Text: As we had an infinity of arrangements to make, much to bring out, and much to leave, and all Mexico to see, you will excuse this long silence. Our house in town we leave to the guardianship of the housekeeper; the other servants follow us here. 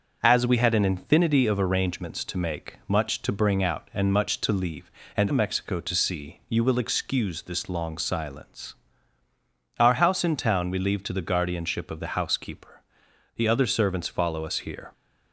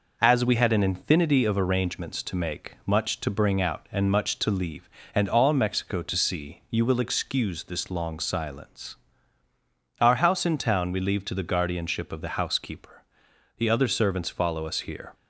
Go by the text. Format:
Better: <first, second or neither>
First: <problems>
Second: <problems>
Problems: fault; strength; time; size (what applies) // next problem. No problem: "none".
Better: second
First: starts louder than the rest; until 1.2 s; 6.5 dB // skips "all"; at 5.3 s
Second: none